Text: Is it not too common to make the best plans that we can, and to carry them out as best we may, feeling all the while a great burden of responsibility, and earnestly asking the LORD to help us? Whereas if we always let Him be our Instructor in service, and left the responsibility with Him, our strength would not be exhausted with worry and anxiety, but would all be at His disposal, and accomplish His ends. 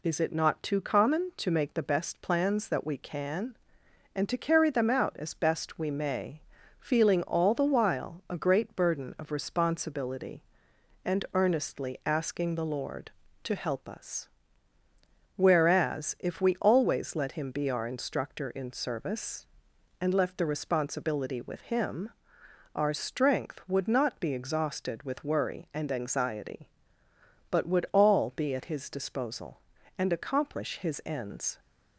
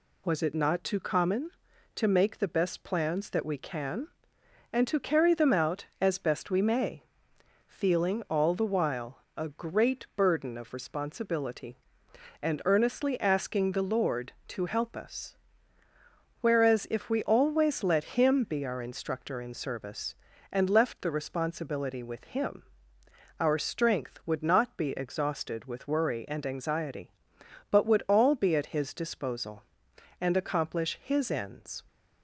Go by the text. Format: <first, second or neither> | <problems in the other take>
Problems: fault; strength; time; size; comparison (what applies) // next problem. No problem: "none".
first | says "Was" for "Is"; at 0.2 s // pauses between "while" and "a"; slight; at 9.1 s; 0.18 s long